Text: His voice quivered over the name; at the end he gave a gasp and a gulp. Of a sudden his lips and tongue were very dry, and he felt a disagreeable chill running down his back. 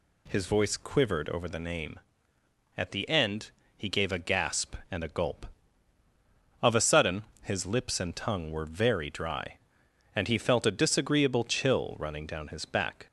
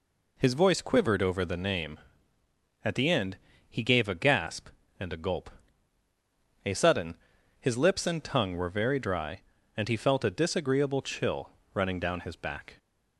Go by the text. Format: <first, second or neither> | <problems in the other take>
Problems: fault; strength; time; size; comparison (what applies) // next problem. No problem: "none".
first | pauses between "end" and "he"; slight; at 3.3 s; 0.30 s long; slight in the first // skips "Of"; at 6.0 s // pauses between "sudden" and "his"; at 7.1 s; 0.44 s long; slight in the first // pauses between "chill" and "running"; slight; at 11.4 s; 0.24 s long